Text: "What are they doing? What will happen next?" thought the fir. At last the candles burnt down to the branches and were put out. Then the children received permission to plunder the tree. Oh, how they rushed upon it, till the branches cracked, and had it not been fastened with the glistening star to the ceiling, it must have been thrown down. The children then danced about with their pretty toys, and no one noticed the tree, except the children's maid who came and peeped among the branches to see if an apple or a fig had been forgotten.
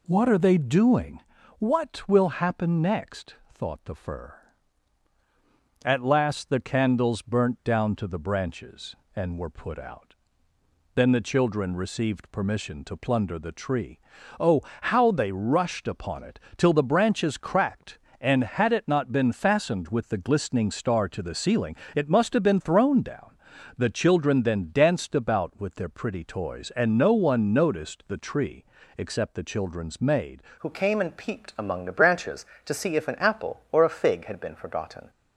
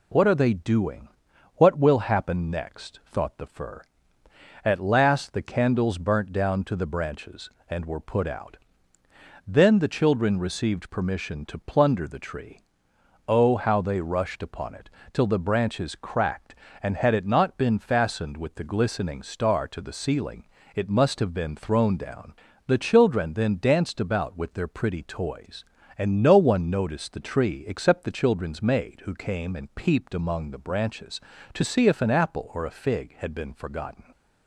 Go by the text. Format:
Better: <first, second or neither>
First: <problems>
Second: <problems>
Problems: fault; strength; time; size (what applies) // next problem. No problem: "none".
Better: second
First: changes voice at "who"; from 30.5 s on; 4.5 s long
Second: none